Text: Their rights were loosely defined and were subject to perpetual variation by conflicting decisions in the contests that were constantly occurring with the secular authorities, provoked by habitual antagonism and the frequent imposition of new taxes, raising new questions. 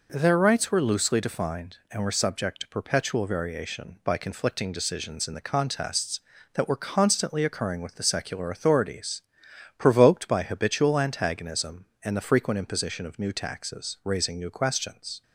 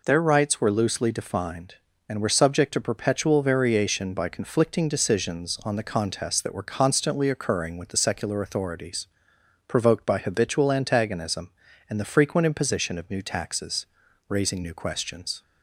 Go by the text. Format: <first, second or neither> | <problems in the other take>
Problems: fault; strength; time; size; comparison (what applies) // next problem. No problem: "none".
first | says "on" for "in"; at 5.6 s